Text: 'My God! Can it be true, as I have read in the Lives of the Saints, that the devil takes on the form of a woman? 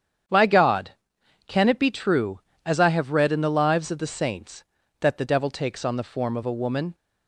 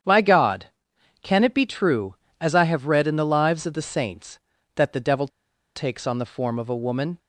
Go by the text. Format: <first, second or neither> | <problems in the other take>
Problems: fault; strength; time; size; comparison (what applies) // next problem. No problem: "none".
first | starts louder than the rest; strong; until 1.6 s; 8.5 dB; strong in the first // pauses between "devil" and "takes"; noticeable; at 5.2 s; 0.48 s long